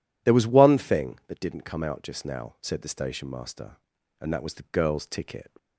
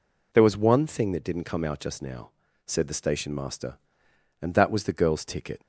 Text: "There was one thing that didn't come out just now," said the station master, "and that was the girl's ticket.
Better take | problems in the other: neither | none

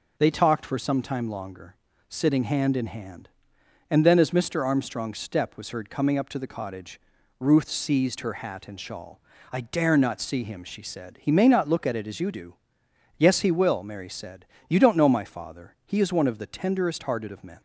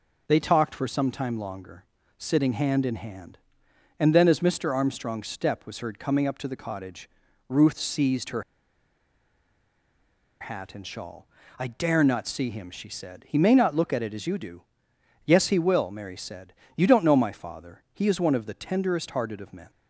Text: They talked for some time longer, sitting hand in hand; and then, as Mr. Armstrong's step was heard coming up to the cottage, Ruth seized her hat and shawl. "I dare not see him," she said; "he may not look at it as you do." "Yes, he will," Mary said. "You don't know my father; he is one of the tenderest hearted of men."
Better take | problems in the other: first | pauses between "her" and "hat"; strong; at 8.4 s; 1.9 s long

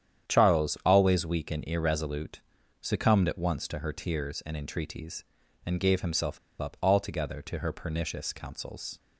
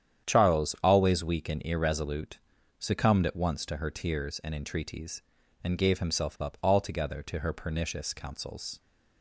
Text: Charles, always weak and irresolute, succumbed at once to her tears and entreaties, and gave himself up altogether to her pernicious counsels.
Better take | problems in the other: second | starts louder than the rest; strong; until 1.3 s; 9.5 dB; strong in the second // pauses between "himself" and "up"; slight; at 6.3 s; 0.22 s long

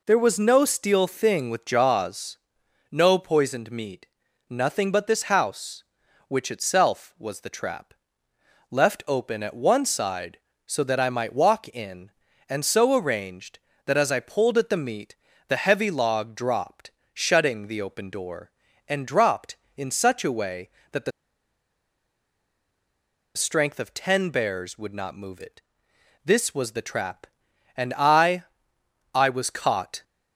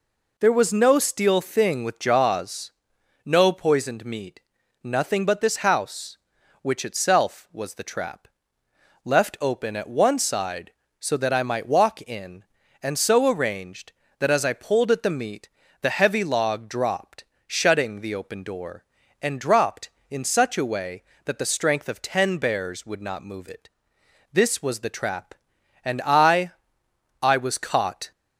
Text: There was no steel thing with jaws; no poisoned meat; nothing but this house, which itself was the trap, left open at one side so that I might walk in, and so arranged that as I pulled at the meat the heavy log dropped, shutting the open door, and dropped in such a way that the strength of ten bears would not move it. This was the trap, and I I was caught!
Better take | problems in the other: second | pauses between "meat" and "the"; slight; at 15.1 s; 0.32 s long; slight in the second // pauses between "the" and "strength"; strong; at 21.1 s; 2.2 s long // pauses between "I" and "I"; noticeable; at 28.4 s; 0.70 s long; noticeable in the second

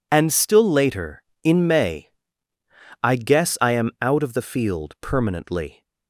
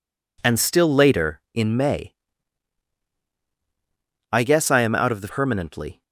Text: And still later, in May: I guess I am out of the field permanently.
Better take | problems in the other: first | skips "field"; at 5.2 s

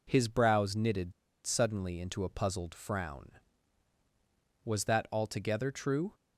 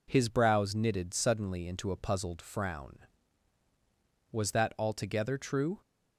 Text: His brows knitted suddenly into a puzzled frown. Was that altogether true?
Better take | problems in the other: second | pauses between "knitted" and "suddenly"; slight; at 1.1 s; 0.33 s long

